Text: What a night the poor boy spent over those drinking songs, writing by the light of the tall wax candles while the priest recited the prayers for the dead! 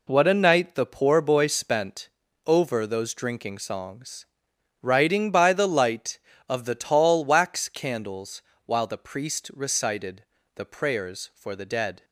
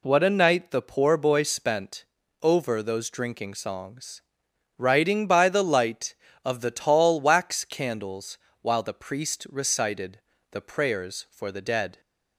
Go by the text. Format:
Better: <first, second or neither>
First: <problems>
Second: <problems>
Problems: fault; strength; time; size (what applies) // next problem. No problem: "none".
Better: second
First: gets quieter; strong; throughout; 9 dB // pauses between "spent" and "over"; at 2.0 s; 0.38 s long // pauses between "candles" and "while"; slight; at 8.4 s; 0.24 s long // pauses between "recited" and "the"; slight; at 10.2 s; 0.32 s long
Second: pauses between "spent" and "over"; at 2.0 s; 0.38 s long // pauses between "candles" and "while"; slight; at 8.3 s; 0.24 s long // pauses between "recited" and "the"; slight; at 10.1 s; 0.32 s long